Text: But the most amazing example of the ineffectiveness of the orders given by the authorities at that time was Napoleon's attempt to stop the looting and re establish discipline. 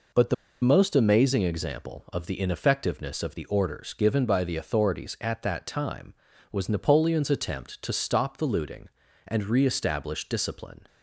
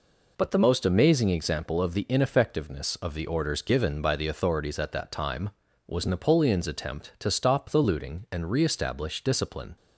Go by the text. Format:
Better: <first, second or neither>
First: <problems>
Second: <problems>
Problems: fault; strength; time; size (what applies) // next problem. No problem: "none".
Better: second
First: pauses between "the" and "most"; slight; at 0.3 s; 0.27 s long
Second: none